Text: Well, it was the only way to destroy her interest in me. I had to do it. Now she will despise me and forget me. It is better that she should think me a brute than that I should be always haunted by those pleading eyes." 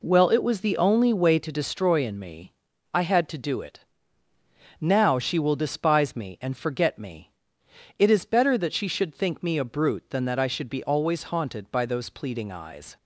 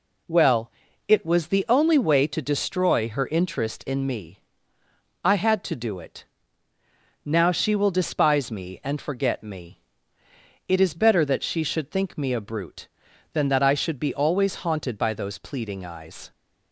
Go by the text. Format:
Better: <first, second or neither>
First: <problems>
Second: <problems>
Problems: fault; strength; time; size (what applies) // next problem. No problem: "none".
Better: second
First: skips "her interest"; at 2.0 s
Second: none